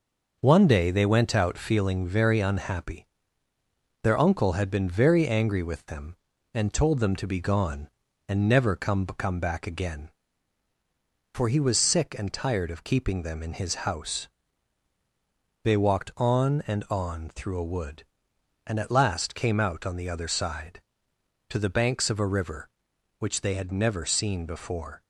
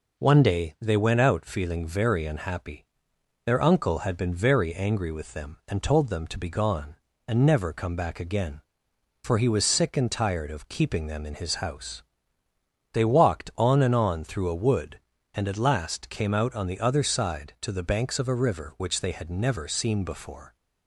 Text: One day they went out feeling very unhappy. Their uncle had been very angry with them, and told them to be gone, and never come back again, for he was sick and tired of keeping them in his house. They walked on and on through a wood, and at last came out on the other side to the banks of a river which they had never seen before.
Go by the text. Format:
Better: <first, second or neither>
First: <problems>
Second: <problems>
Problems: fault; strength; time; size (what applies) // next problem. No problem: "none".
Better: second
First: says "come" twice; at 9.0 s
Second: none